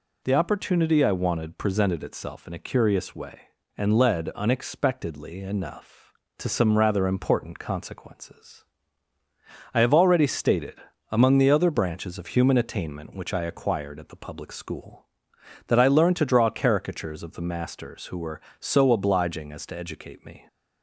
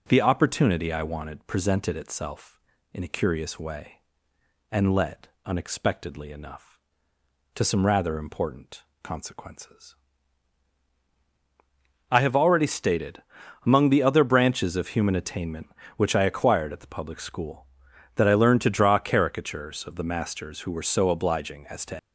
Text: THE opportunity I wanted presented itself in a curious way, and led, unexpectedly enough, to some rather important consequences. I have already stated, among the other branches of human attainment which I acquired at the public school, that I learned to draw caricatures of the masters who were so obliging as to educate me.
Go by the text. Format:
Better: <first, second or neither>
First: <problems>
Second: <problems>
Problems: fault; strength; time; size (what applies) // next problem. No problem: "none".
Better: first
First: none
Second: pauses between "important" and "consequences"; slight; at 8.8 s; 0.20 s long // stops before "educate me"; at 21.9 s